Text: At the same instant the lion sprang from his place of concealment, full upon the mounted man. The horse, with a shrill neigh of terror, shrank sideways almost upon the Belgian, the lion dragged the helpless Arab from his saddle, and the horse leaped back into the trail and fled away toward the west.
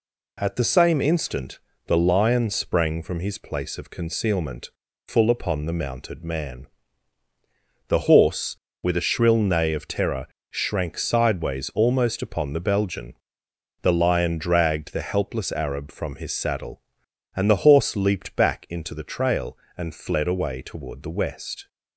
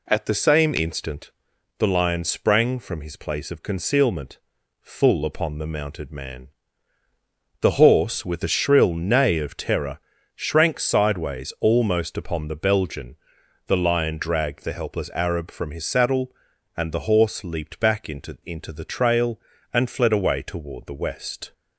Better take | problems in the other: first | pauses between "instant" and "the"; noticeable; at 1.3 s; 0.48 s long; slight in the first // says "into" twice; at 18.4 s

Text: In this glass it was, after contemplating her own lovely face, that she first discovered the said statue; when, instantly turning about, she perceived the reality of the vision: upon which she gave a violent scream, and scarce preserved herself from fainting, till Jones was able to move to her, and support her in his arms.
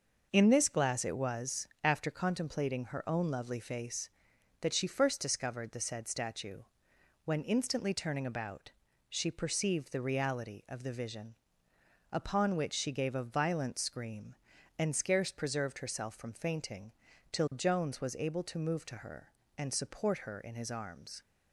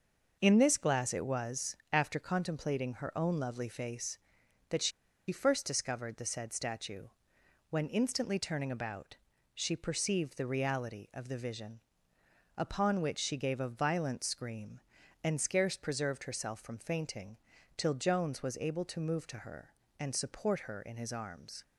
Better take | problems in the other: first | pauses between "she" and "first"; at 4.9 s; 0.39 s long

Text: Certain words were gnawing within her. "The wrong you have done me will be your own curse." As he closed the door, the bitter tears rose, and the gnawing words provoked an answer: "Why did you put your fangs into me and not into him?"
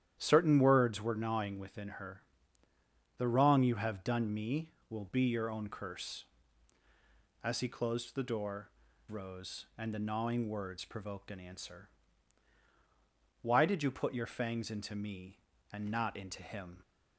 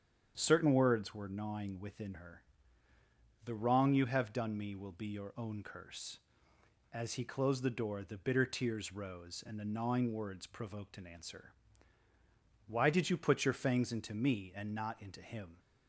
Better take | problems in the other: second | starts louder than the rest; strong; until 1.2 s; 10.5 dB; strong in the second // skips "the bitter tears"; at 8.9 s

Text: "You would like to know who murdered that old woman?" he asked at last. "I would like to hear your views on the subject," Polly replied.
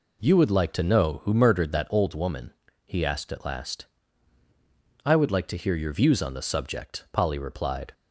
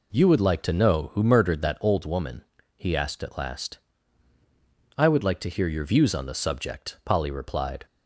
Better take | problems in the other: neither | none

